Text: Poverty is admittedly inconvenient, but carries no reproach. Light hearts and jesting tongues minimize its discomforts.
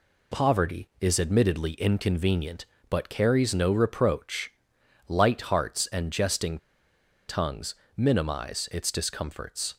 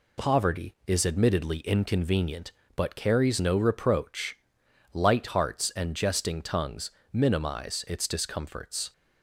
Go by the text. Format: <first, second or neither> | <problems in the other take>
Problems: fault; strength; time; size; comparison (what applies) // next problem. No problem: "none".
second | pauses between "jesting" and "tongues"; noticeable; at 6.5 s; 0.70 s long // pauses between "tongues" and "minimize"; slight; at 7.7 s; 0.22 s long; slight in the second